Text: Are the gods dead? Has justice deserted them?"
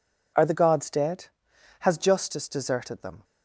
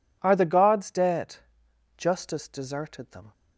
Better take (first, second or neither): first